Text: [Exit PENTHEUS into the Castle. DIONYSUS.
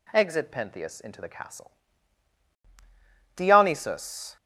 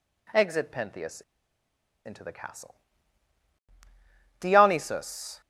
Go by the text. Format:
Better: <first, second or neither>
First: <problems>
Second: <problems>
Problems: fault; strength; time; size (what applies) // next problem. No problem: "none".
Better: first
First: none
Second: pauses between "PENTHEUS" and "into"; noticeable; at 1.2 s; 0.84 s long